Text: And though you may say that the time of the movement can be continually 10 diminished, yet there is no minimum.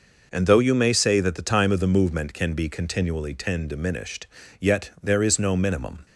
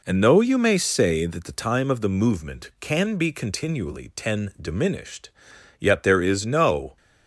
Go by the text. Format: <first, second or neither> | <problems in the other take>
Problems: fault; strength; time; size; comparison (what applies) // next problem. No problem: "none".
first | stops before "minimum"; at 6.9 s